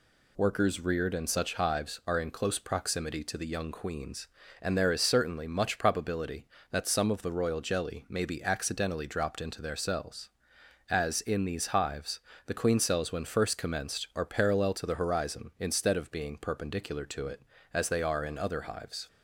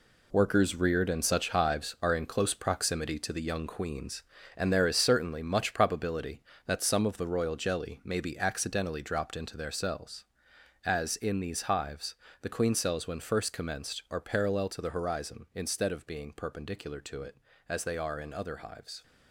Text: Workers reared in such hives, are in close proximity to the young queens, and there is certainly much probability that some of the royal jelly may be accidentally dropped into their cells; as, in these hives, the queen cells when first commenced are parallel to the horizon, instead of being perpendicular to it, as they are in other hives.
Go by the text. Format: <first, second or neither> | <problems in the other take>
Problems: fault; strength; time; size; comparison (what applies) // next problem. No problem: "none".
first | gets quieter; strong; throughout; 9 dB